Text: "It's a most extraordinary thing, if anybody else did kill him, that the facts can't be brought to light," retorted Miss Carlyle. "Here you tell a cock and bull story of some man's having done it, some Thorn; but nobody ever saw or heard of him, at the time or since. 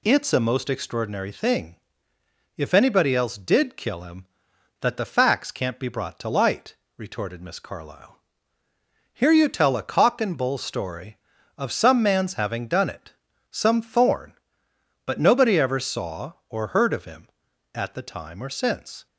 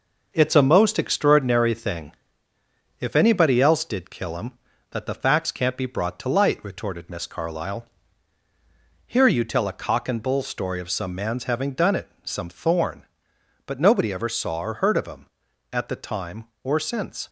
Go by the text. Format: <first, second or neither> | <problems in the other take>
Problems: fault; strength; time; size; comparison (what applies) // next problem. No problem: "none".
first | gets quieter; noticeable; throughout; 4.5 dB